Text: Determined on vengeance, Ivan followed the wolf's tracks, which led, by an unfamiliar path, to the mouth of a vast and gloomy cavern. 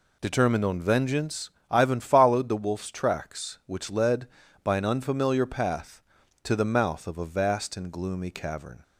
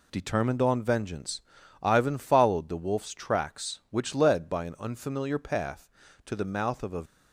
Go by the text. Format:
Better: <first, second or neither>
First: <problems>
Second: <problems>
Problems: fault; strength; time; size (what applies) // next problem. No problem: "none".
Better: first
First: none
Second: stops before "vast and gloomy cavern"; at 7.0 s